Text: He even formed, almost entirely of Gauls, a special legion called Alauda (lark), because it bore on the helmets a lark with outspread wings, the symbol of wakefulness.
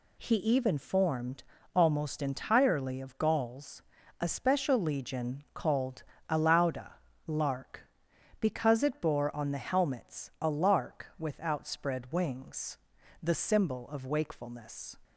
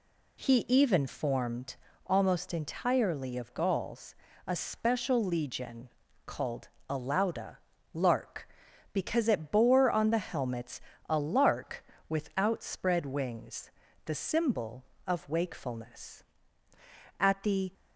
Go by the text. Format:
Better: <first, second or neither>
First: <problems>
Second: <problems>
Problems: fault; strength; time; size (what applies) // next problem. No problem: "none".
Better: first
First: pauses between "called" and "Alauda"; slight; at 6.0 s; 0.26 s long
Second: pauses between "legion" and "called"; at 5.8 s; 0.38 s long // pauses between "called" and "Alauda"; slight; at 6.6 s; 0.20 s long // pauses between "helmets" and "a"; slight; at 10.7 s; 0.30 s long // goes on to say "At the"; from 17.1 s on; 0.54 s long